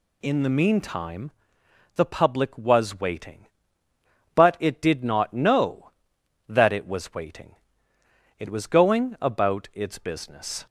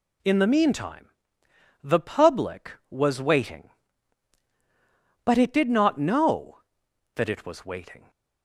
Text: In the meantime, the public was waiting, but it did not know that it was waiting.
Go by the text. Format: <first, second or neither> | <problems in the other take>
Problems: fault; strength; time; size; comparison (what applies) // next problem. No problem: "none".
second | goes on to say "It was going about its business"; strong; from 8.3 s on; 2.2 s long